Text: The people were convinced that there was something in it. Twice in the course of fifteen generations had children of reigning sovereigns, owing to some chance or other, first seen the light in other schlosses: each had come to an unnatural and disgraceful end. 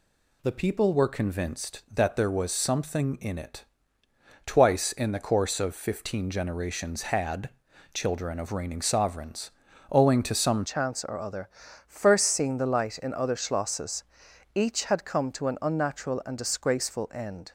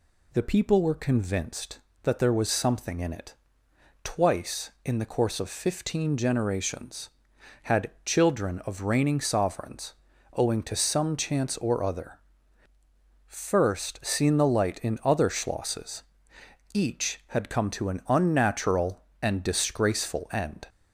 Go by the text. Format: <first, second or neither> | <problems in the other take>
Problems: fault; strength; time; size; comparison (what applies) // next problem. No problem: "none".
second | pauses between "had" and "children"; at 7.4 s; 0.44 s long // changes voice at "chance"; from 10.6 s on; 6.9 s long